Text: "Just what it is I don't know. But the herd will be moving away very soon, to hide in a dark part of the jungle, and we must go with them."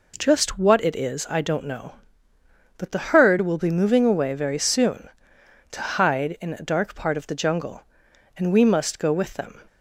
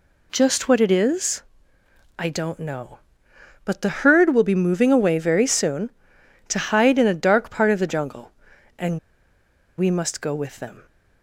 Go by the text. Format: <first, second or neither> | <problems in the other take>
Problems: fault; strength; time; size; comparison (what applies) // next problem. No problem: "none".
first | pauses between "is" and "I"; noticeable; at 1.4 s; 0.74 s long // pauses between "and" and "we"; noticeable; at 8.9 s; 0.79 s long